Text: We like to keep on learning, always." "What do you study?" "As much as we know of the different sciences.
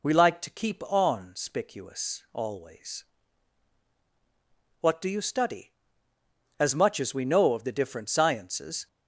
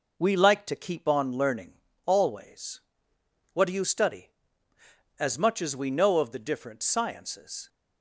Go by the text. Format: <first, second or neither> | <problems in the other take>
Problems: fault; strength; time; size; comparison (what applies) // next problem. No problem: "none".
second | says "spicuous" for "learning"; at 1.3 s